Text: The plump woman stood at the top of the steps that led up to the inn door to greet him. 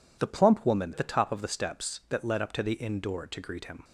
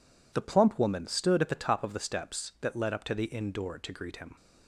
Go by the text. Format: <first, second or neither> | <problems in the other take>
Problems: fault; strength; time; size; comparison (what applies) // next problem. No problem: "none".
second | skips "stood"; at 0.9 s